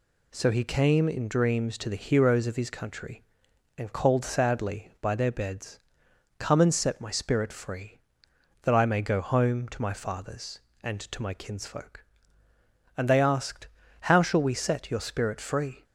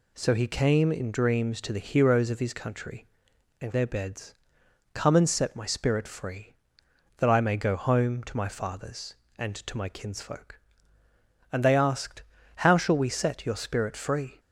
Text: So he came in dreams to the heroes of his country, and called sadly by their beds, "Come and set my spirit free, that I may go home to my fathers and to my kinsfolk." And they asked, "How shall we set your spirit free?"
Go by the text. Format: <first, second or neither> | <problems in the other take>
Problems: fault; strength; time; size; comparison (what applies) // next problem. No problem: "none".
first | skips "called sadly by"; at 3.7 s